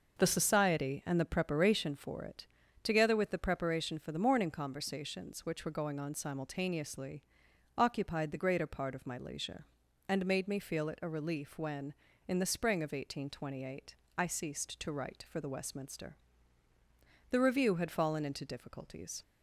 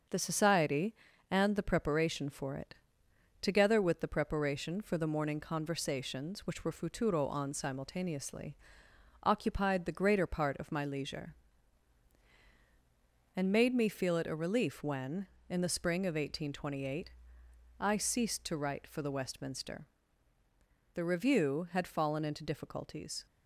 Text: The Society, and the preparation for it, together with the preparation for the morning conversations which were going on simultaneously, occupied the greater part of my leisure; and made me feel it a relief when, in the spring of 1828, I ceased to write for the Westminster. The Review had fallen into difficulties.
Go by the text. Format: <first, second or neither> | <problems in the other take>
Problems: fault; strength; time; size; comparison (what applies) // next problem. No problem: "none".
first | starts louder than the rest; until 1.4 s; 6.5 dB // says "futuro" for "going"; at 6.7 s